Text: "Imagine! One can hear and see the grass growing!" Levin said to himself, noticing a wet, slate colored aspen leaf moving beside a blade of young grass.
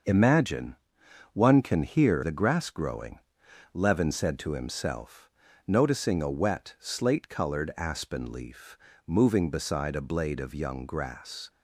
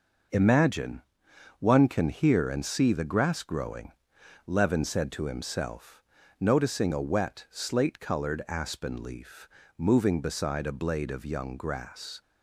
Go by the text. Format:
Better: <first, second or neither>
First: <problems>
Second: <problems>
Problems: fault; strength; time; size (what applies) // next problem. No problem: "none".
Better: second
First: starts louder than the rest; until 1.6 s; 6.5 dB // skips "and see"; at 2.2 s // pauses between "leaf" and "moving"; slight; at 8.7 s; 0.30 s long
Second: pauses between "leaf" and "moving"; slight; at 9.4 s; 0.30 s long